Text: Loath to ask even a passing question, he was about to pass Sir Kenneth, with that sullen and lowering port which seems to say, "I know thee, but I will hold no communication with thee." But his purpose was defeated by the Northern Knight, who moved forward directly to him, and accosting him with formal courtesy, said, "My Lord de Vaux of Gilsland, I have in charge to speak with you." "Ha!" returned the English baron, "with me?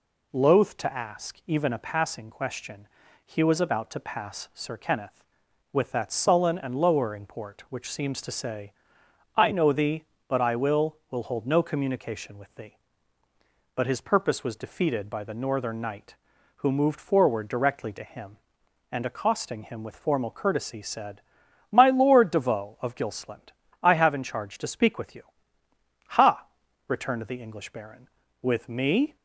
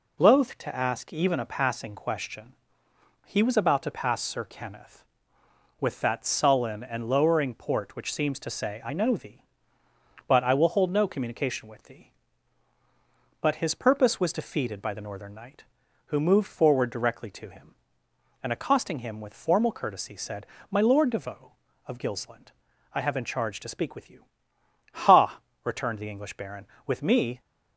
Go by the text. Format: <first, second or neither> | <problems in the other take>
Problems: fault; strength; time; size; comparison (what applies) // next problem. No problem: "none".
second | says "will" twice; at 11.0 s